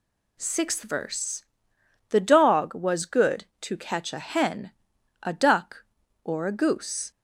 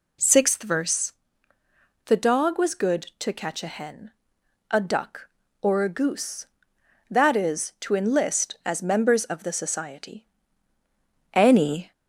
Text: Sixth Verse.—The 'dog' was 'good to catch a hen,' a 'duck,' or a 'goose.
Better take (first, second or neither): first